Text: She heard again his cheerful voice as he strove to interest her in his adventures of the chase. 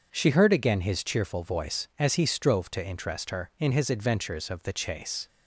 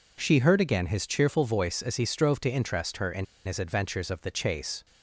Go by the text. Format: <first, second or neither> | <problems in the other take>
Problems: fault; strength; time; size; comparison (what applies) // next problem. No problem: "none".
first | pauses between "in" and "his"; slight; at 3.2 s; 0.20 s long